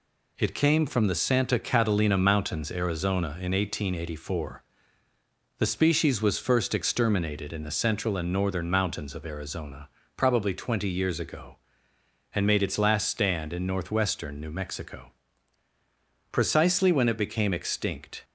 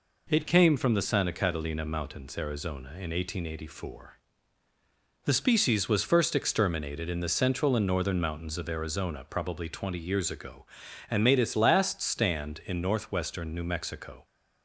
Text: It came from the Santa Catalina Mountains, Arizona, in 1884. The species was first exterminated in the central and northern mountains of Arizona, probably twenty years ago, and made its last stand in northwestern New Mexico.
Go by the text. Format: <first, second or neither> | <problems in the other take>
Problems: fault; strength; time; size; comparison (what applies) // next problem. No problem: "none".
second | goes on to say "Precisely when it became extinct"; strong; from 16.3 s on; 1.9 s long